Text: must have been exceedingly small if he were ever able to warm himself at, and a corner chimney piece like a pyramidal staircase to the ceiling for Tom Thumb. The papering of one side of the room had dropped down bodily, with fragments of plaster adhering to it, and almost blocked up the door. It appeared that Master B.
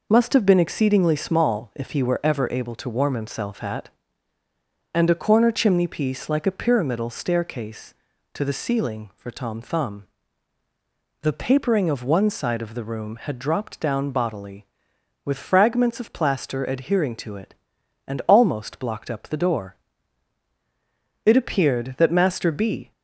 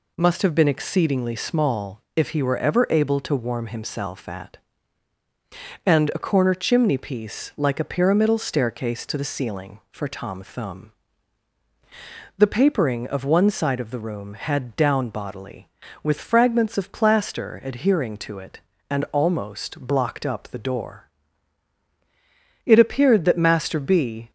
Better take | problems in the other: first | pauses between "small" and "if"; slight; at 2.0 s; 0.16 s long // skips "dropped"; at 14.7 s

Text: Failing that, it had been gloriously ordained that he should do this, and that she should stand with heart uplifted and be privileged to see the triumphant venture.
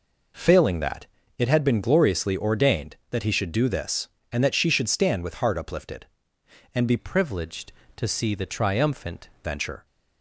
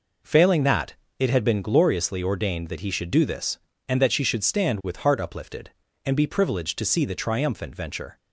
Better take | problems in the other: second | changes voice from "privileged" to "triumphant"; from 6.9 to 9.2 s; 2.3 s long

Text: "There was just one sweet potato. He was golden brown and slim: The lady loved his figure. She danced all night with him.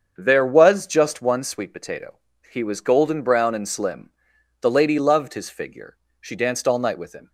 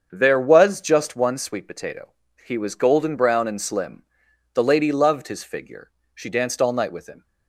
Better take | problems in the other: neither | starts louder than the rest; strong; the same in both

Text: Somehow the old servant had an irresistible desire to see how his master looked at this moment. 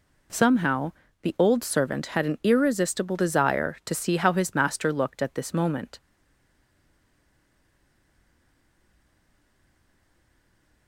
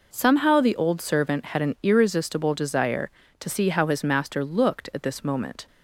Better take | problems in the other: second | pauses between "Somehow" and "the"; slight; at 0.9 s; 0.30 s long // stays silent after the last word; strong; from 6.0 s on; 4.8 s long

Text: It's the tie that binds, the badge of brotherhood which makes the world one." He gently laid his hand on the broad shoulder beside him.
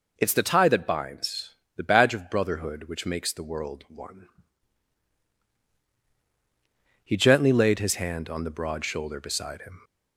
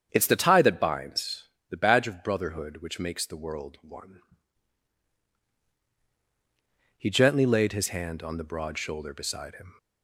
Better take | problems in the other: first | starts louder than the rest; strong; until 1.5 s; 8 dB

